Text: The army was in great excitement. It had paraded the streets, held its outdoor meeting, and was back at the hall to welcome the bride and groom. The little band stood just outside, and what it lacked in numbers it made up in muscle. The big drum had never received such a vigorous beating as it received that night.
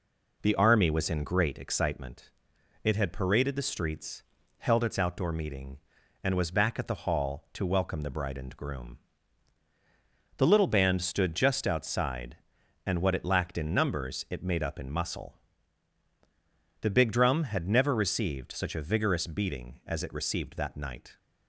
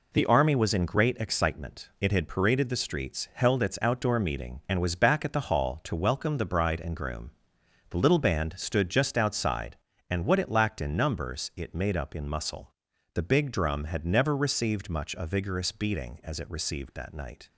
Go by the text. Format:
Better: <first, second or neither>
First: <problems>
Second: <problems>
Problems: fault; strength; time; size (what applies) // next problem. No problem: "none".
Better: first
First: none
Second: says "much" for "such"; at 14.8 s